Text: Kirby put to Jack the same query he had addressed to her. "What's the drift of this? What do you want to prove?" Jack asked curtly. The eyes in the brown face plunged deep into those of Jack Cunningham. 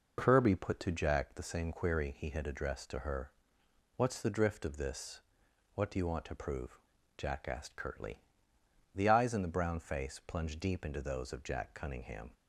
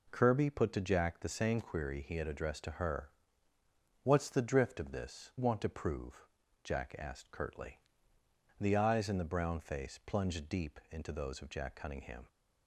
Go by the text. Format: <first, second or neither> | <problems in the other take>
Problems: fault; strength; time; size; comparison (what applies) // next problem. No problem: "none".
first | skips "What do you"; at 5.3 s